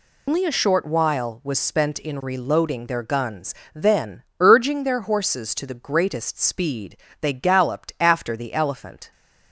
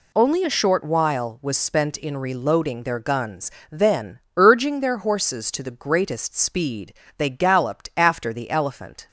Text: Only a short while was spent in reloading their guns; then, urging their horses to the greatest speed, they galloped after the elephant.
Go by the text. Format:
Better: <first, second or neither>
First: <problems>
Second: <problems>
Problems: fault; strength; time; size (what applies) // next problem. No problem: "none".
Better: second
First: loses the start of "Only"; at 0.2 s; 125 ms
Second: none